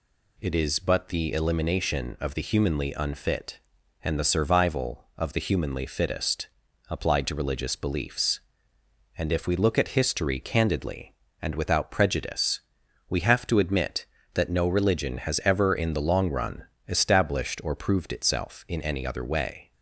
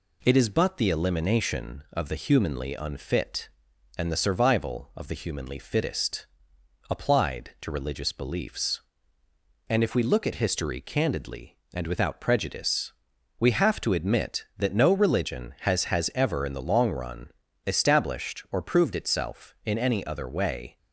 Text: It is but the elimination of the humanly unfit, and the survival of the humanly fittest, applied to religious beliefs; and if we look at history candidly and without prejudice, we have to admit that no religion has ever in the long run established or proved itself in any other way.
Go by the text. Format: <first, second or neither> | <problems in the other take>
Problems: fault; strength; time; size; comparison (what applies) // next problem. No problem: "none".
first | says "has" twice; at 15.8 s // pauses between "run" and "established"; slight; at 17.3 s; 0.34 s long; slight in the first